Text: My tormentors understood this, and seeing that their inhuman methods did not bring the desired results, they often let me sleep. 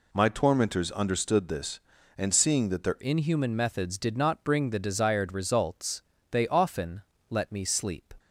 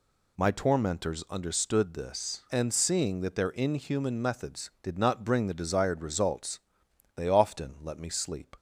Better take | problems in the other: second | changes voice at "inhuman"; from 3.0 s on; 5.1 s long // pauses between "often" and "let"; slight; at 7.0 s; 0.26 s long

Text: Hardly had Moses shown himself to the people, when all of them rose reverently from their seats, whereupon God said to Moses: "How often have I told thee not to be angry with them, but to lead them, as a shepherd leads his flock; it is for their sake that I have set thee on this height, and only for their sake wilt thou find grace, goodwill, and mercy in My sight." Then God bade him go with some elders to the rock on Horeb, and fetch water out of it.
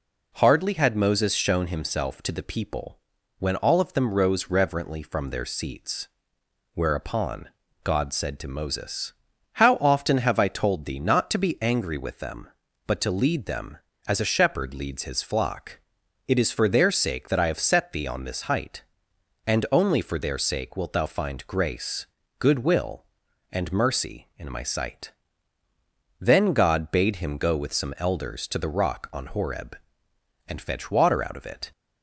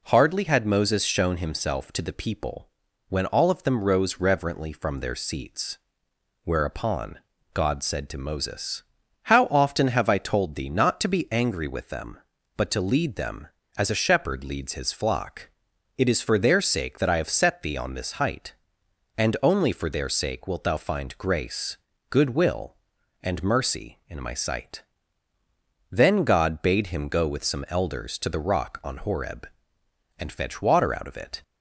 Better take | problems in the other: neither | pauses between "whereupon" and "God"; slight; the same in both

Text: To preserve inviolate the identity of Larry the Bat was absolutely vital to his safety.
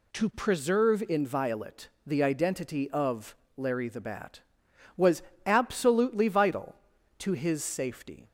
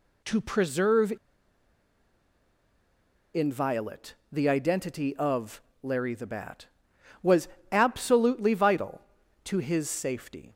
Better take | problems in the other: first | pauses between "preserve" and "inviolate"; strong; at 1.1 s; 2.2 s long // pauses between "inviolate" and "the"; slight; at 4.1 s; 0.16 s long; slight in the first // pauses between "of" and "Larry"; slight; at 5.6 s; 0.22 s long; slight in the first // pauses between "was" and "absolutely"; slight; at 7.4 s; 0.22 s long; slight in the first

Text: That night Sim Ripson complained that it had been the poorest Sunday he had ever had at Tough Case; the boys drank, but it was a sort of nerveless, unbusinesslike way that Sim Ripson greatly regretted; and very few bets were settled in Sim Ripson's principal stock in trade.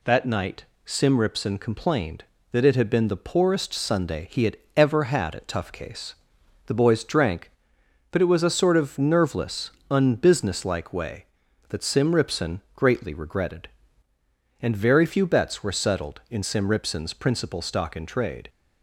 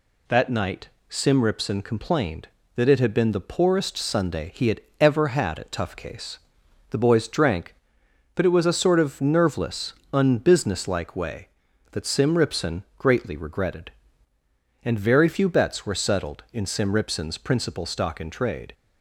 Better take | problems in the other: neither | pauses between "night" and "Sim"; slight; the same in both // pauses between "had" and "ever"; slight; the same in both

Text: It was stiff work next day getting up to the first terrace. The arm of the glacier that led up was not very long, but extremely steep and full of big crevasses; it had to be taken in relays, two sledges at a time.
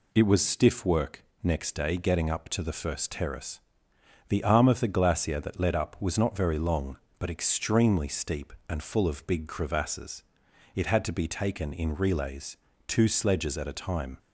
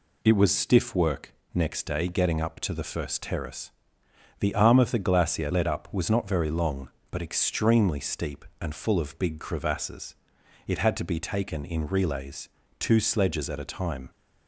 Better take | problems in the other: first | pauses between "work" and "next"; slight; at 1.3 s; 0.18 s long; slight in the first // skips "that"; at 5.5 s

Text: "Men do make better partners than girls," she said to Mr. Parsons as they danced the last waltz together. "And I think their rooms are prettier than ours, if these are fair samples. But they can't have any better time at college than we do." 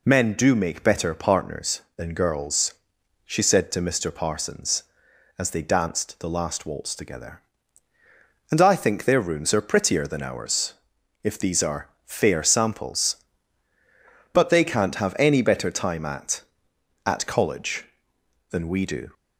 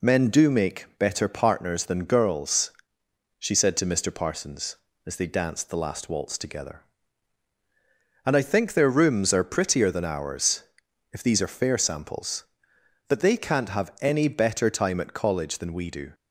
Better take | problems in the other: second | pauses between "are" and "fair"; slight; at 11.8 s; 0.16 s long // says "at" twice; at 17.0 s

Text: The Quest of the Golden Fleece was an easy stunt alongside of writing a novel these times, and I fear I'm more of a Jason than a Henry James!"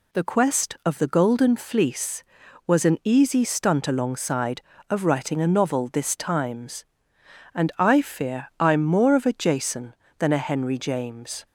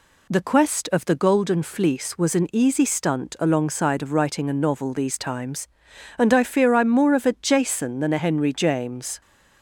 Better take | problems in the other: second | says "this" for "these"; at 5.9 s

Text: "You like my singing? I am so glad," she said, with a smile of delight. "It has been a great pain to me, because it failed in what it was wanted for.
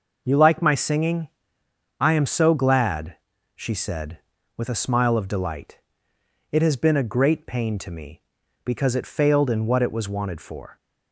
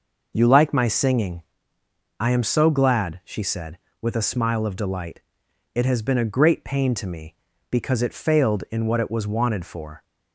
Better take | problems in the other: neither | none

